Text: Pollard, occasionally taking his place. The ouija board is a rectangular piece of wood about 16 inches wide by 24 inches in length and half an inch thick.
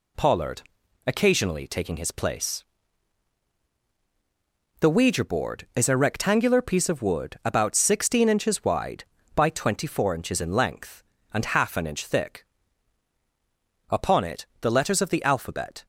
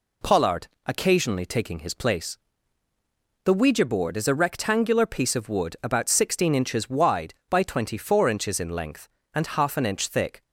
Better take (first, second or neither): second